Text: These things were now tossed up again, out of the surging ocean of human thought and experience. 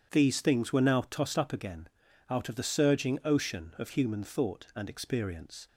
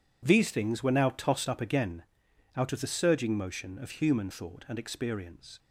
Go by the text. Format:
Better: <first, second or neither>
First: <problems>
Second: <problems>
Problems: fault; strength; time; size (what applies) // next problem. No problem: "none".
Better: first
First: none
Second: says "motion" for "ocean"; at 3.3 s